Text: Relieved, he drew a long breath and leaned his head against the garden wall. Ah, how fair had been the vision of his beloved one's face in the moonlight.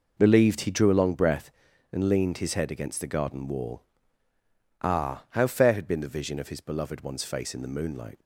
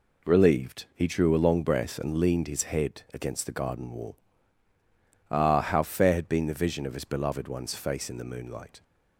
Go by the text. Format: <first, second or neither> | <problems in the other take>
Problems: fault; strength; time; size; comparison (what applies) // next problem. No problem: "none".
neither | none